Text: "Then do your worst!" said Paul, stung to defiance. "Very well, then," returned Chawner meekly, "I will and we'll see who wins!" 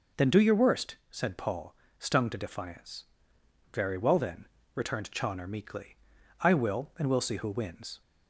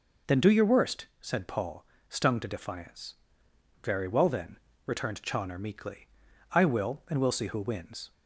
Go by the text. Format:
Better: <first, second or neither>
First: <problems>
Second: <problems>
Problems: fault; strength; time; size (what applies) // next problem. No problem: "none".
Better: neither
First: none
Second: none